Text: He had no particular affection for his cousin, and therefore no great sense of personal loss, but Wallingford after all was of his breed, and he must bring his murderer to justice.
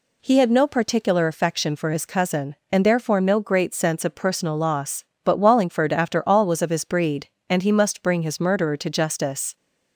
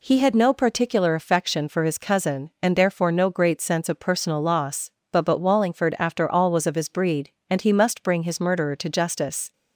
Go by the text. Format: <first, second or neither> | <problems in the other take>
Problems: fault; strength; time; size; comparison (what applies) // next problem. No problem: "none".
first | says "but" twice; at 5.2 s